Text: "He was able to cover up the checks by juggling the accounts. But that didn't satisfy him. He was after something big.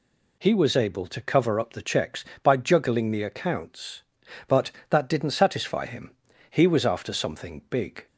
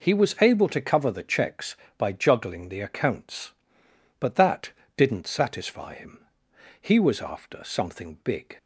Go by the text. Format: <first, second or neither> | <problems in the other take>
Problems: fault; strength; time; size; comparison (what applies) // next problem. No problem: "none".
first | skips "up"; at 1.1 s // pauses between "that" and "didn't"; slight; at 4.7 s; 0.26 s long